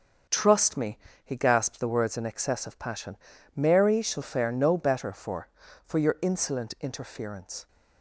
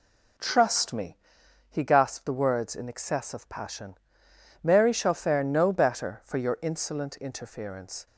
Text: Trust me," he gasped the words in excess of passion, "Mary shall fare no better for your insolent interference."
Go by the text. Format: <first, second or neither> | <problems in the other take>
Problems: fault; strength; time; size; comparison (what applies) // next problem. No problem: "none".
second | starts louder than the rest; until 1.5 s; 6.5 dB // says "for" twice; at 5.8 s